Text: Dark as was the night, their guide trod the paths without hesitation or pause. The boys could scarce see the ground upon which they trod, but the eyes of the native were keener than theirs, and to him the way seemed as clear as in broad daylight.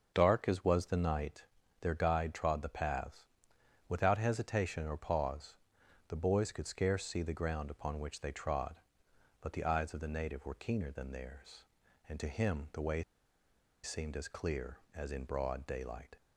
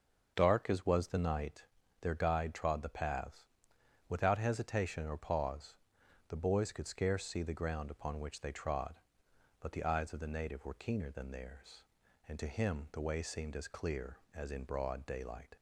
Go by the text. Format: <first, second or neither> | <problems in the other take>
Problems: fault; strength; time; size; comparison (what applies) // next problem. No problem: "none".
second | starts louder than the rest; until 1.1 s; 6.5 dB; also in the second // pauses between "paths" and "without"; noticeable; at 3.2 s; 0.64 s long; noticeable in the second // pauses between "way" and "seemed"; noticeable; at 13.0 s; 0.81 s long